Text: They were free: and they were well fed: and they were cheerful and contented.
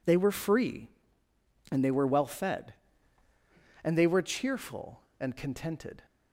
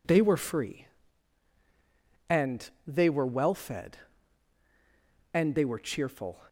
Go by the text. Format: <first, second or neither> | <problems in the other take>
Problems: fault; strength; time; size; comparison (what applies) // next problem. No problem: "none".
first | pauses between "and" and "they"; slight; at 2.6 s; 0.18 s long // stops before "and contented"; at 6.4 s